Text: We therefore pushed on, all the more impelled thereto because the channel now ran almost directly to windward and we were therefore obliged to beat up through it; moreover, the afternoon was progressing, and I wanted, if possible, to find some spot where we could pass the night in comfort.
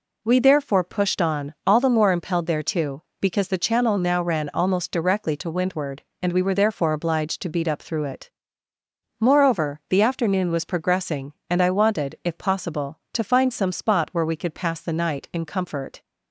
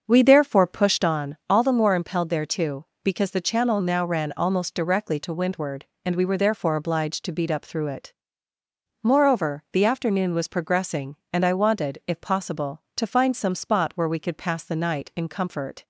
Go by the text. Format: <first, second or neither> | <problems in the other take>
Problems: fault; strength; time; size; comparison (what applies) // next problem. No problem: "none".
first | starts louder than the rest; until 1.2 s; 6.5 dB